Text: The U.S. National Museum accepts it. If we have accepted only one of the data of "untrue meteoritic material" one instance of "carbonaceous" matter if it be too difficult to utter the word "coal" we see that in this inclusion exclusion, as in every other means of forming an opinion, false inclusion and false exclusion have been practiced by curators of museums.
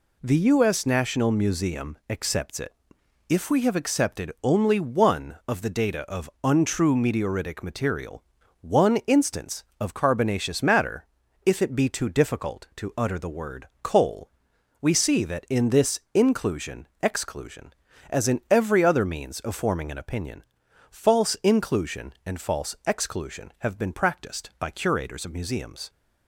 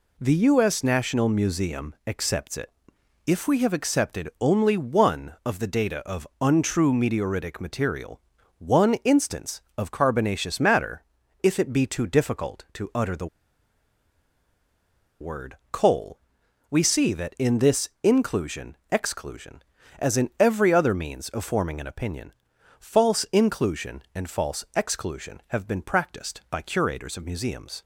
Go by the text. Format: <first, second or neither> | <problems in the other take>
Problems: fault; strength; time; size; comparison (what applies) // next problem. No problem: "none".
first | pauses between "material" and "one"; at 8.1 s; 0.40 s long; also in the first // pauses between "matter" and "if"; at 11.0 s; 0.40 s long; also in the first // pauses between "the" and "word"; strong; at 13.2 s; 1.9 s long // pauses between "coal" and "we"; noticeable; at 16.1 s; 0.50 s long; noticeable in the first